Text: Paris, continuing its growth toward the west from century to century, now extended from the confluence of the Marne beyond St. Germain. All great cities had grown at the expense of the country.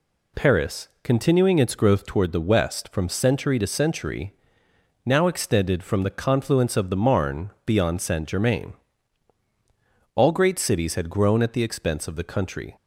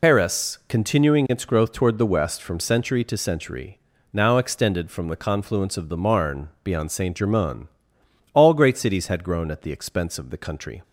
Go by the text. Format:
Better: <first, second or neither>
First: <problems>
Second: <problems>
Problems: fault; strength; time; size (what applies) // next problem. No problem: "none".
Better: first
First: none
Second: loses the start of "Paris"; at 0.0 s; 55 ms // pauses between "Marne" and "beyond"; slight; at 6.4 s; 0.16 s long